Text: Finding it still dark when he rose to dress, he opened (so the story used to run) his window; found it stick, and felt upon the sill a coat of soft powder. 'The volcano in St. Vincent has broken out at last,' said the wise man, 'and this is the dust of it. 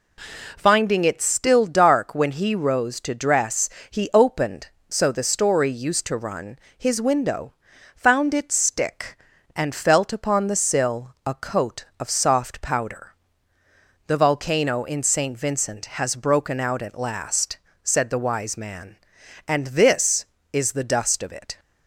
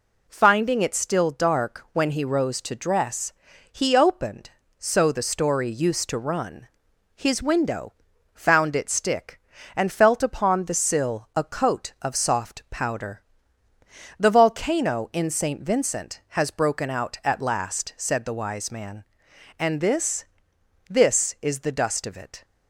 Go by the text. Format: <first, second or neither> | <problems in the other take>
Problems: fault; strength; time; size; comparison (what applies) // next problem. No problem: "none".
first | says "this" twice; at 20.9 s